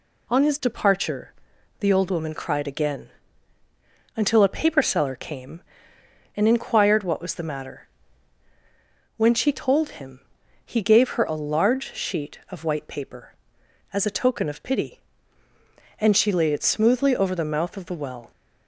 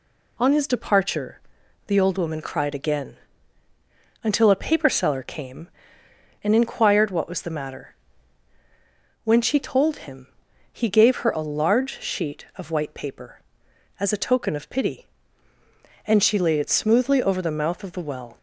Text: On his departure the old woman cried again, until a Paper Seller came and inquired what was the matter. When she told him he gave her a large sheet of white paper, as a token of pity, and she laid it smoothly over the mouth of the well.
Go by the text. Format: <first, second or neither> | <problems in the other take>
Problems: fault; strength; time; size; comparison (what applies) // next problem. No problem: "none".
neither | pauses between "departure" and "the"; noticeable; the same in both // pauses between "him" and "he"; noticeable; the same in both